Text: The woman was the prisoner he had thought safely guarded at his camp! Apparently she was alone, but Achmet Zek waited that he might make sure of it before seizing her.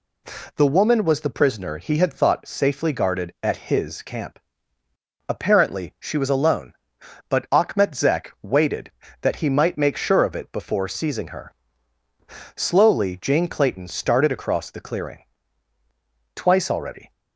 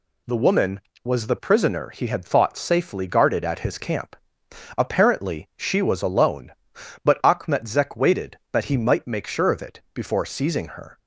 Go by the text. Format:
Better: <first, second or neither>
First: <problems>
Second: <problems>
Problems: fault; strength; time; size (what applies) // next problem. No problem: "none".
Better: second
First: goes on to say "Slowly Jane Clayton started across the clearing Twice already"; strong; from 12.5 s on; 4.5 s long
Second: none